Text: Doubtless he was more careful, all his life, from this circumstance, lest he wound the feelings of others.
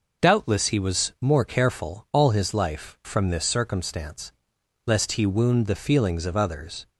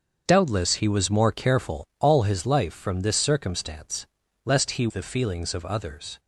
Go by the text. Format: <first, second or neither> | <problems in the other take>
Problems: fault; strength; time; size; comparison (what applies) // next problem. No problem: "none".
first | starts louder than the rest; until 1.2 s; 7 dB // skips "wound"; at 4.8 s